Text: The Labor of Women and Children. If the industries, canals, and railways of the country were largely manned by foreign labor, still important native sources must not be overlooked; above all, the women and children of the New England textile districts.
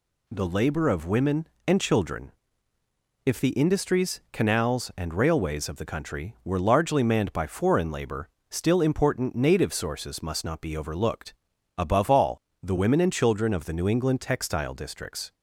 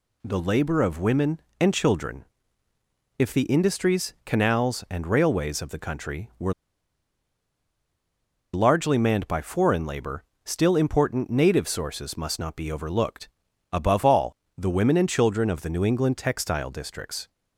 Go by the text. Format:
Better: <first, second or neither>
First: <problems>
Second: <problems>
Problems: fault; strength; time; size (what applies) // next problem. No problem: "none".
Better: first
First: none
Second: pauses between "were" and "largely"; strong; at 6.5 s; 2.0 s long